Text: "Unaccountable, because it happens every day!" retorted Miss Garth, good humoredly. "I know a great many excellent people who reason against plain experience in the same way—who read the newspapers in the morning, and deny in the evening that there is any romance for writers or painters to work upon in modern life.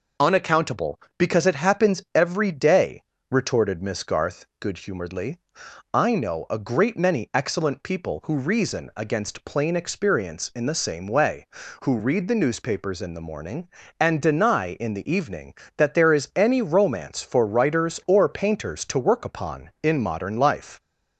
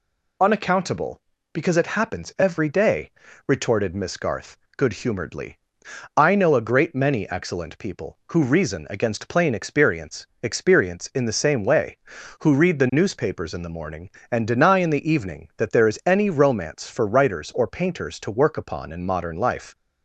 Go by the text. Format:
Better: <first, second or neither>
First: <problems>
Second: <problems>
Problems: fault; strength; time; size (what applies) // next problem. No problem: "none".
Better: first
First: none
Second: says "experience" twice; at 10.4 s